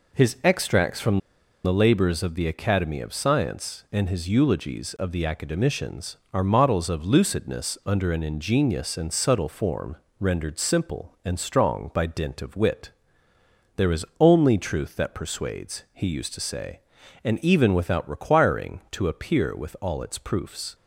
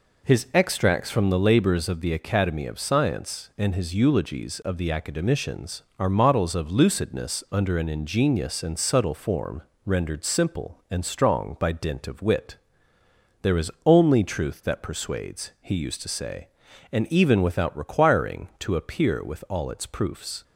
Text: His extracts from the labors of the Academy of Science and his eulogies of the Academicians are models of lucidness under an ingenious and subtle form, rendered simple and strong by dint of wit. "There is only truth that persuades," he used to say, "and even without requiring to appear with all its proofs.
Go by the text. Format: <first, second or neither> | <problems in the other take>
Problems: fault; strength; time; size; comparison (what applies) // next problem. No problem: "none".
second | pauses between "from" and "the"; noticeable; at 1.1 s; 0.46 s long